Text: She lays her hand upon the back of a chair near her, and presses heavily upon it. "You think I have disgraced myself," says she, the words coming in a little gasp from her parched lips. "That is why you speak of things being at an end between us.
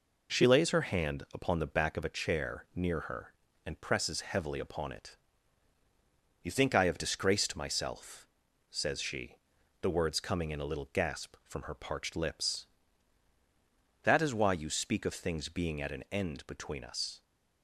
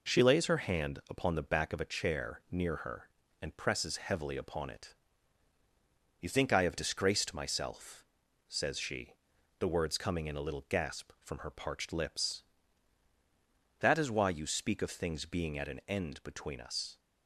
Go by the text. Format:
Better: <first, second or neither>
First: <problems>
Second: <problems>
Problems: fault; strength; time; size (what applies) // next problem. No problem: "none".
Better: neither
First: none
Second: none